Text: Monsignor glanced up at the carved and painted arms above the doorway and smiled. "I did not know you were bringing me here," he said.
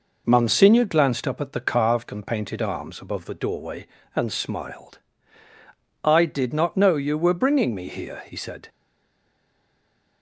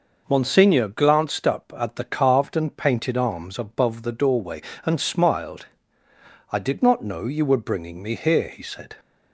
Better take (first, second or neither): second